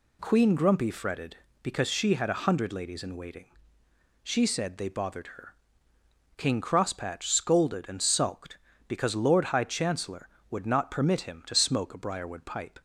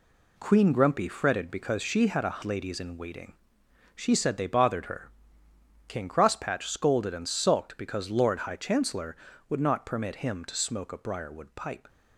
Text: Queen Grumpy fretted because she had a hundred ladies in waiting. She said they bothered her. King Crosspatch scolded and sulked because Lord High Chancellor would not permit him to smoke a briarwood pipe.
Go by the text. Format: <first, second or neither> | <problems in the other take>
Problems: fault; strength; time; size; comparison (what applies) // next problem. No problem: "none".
first | skips "hundred"; at 2.4 s